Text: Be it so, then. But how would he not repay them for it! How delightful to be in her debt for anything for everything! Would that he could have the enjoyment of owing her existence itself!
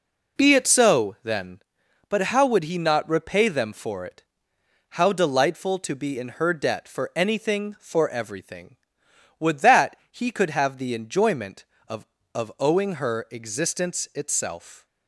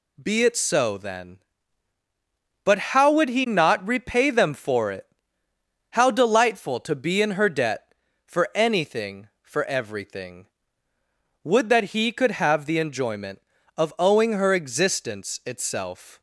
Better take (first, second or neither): second